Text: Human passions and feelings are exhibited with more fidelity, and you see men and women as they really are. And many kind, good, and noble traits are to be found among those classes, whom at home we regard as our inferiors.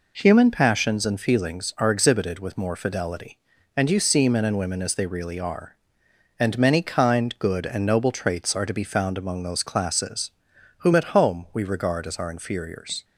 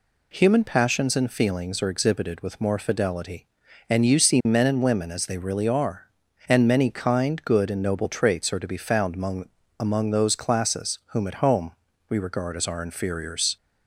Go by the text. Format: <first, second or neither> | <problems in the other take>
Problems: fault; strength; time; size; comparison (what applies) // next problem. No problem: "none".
first | says "among" twice; at 9.8 s // pauses between "home" and "we"; at 11.7 s; 0.38 s long